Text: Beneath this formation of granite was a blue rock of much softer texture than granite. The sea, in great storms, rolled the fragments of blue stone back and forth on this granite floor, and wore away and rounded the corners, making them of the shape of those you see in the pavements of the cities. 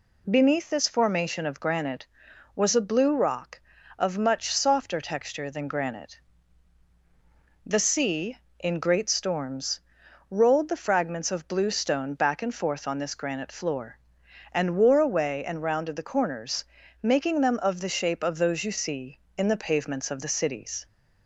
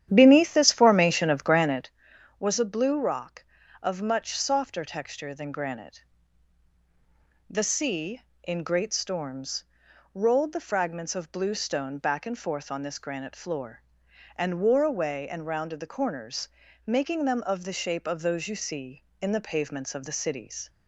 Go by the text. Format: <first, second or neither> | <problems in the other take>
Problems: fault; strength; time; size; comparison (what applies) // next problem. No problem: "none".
first | starts louder than the rest; strong; until 2.0 s; 10.5 dB